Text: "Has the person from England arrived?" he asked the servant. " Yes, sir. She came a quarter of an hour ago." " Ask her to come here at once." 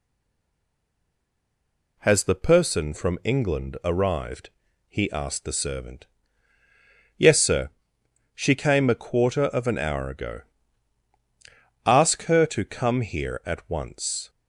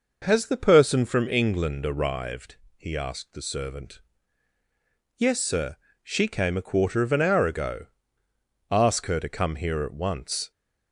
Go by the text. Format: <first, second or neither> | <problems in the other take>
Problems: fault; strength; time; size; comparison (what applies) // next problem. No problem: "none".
second | stays silent before the first word; noticeable; until 1.9 s; 1.9 s long